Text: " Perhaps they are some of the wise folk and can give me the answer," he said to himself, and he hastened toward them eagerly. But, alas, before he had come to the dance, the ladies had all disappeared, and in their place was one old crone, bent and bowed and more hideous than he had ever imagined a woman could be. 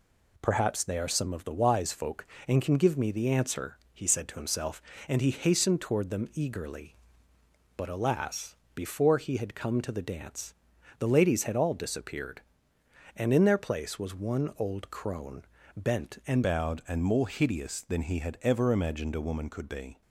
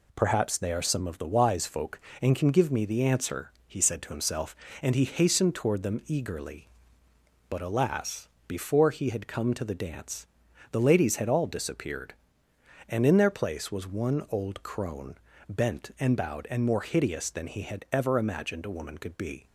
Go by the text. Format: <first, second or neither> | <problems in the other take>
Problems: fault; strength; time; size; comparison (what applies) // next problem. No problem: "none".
second | changes voice at "bowed"; from 16.4 s on; 3.6 s long